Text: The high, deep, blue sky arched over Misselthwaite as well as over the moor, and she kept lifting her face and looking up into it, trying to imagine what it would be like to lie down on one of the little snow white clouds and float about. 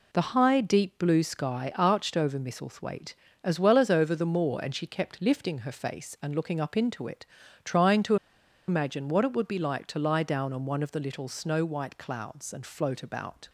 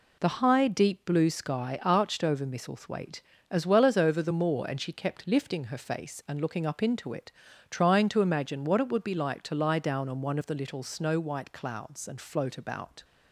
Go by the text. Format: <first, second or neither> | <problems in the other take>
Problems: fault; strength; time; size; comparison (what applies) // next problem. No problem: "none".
second | pauses between "to" and "imagine"; noticeable; at 8.1 s; 0.52 s long